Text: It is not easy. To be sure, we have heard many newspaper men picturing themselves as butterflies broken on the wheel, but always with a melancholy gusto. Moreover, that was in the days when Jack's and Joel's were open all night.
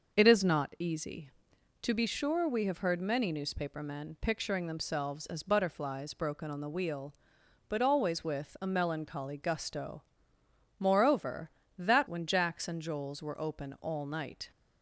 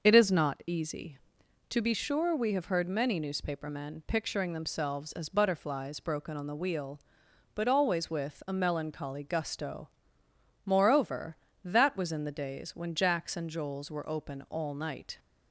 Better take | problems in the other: second | starts louder than the rest; noticeable; until 1.1 s; 6 dB; noticeable in the second // skips "was in the days"; at 12.0 s

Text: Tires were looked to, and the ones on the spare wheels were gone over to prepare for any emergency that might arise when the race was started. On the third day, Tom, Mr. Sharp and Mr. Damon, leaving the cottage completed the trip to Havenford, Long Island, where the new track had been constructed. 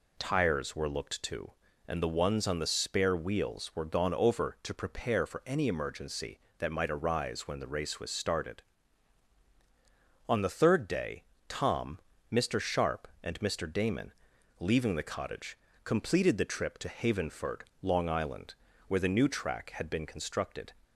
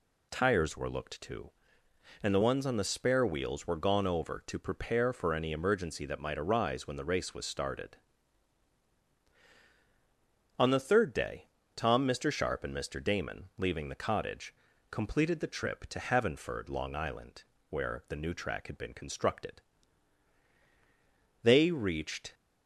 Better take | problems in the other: first | pauses between "cottage" and "completed"; slight; at 14.5 s; 0.36 s long; slight in the first // goes on to say "They reached"; noticeable; from 21.4 s on; 0.92 s long

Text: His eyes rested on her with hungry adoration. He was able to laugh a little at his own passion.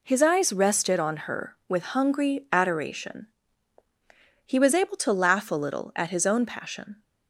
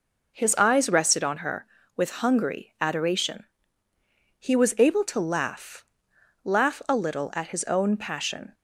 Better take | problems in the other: first | says "laugh" twice; at 6.4 s

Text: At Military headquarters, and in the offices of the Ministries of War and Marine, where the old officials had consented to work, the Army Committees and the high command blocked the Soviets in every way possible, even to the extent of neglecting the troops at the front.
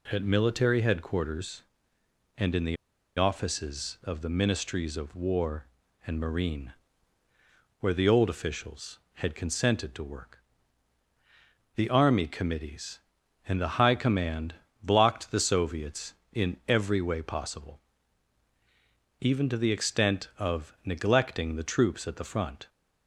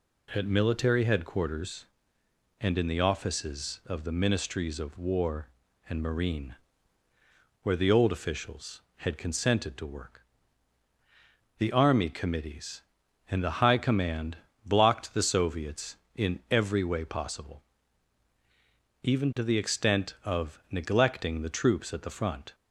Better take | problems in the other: second | pauses between "the" and "offices"; at 2.7 s; 0.40 s long // pauses between "command" and "blocked"; slight; at 14.5 s; 0.26 s long; slight in the second

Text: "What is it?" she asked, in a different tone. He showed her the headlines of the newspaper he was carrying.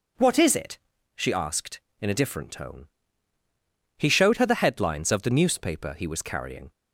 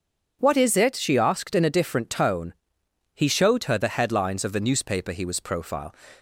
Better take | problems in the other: first | says "profile" for "carrying"; at 5.3 s

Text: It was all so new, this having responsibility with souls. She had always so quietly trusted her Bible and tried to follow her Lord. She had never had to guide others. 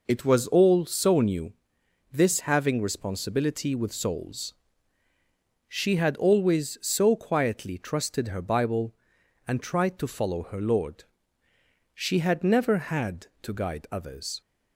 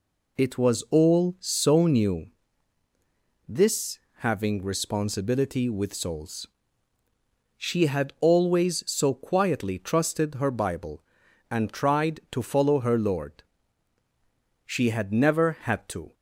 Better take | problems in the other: first | pauses between "this" and "having"; slight; at 3.9 s; 0.16 s long // stops before "guide others"; at 16.1 s

